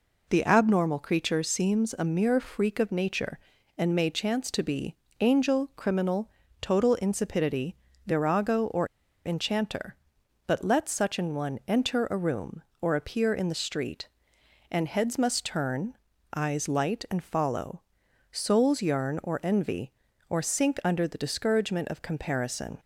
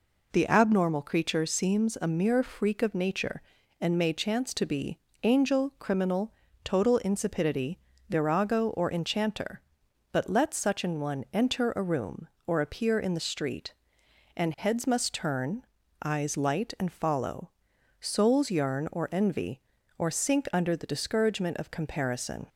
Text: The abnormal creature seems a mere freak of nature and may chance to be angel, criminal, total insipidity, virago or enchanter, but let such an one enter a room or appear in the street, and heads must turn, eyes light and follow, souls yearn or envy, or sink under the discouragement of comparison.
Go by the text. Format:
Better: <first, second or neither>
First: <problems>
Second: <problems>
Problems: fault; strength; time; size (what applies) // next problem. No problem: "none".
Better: second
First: pauses between "be" and "angel"; slight; at 4.9 s; 0.26 s long // pauses between "or" and "enchanter"; at 8.8 s; 0.38 s long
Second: pauses between "be" and "angel"; slight; at 4.9 s; 0.26 s long